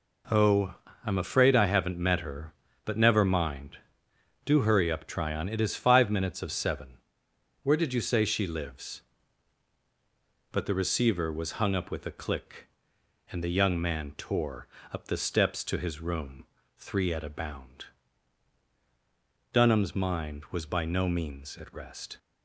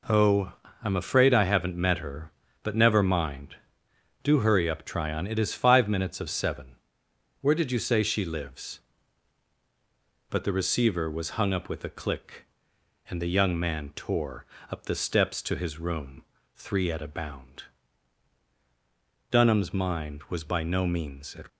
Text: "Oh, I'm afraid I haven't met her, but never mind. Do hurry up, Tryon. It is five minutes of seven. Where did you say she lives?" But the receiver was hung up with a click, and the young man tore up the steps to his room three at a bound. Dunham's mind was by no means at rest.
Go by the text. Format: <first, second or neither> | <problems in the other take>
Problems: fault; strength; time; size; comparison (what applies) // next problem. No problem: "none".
first | pauses between "tore" and "up"; slight; at 14.4 s; 0.26 s long; slight in the first // pauses between "room" and "three"; slight; at 16.2 s; 0.30 s long; slight in the first // stops before "rest"; at 21.4 s